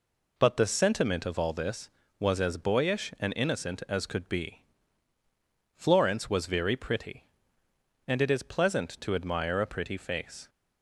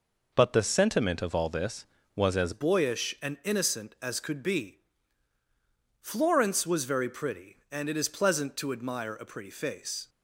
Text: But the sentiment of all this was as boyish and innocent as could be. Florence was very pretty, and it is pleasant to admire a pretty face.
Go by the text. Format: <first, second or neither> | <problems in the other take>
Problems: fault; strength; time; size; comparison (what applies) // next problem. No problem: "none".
first | changes voice at "boyish"; from 2.5 s on; 7.5 s long